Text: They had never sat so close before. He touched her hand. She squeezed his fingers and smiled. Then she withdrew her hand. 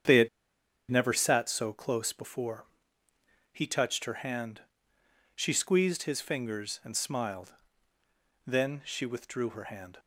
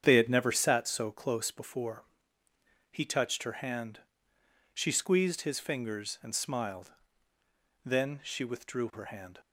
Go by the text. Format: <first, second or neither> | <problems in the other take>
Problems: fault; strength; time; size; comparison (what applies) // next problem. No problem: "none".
second | starts louder than the rest; strong; until 1.6 s; 8 dB; strong in the second // pauses between "had" and "never"; noticeable; at 0.2 s; 0.61 s long